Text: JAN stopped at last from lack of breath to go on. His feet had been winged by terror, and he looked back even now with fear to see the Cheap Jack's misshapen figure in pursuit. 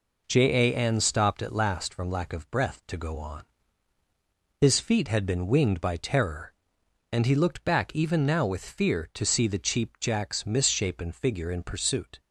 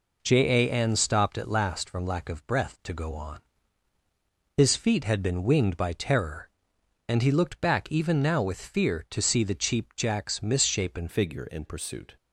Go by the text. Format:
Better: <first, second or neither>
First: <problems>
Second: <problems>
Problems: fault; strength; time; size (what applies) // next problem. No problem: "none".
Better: first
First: none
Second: changes voice at "figure"; from 11.0 s on; 1.1 s long